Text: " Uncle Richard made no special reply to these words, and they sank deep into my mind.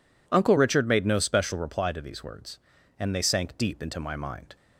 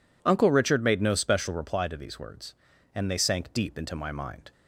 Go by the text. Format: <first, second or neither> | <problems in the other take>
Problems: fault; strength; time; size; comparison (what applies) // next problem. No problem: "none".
neither | none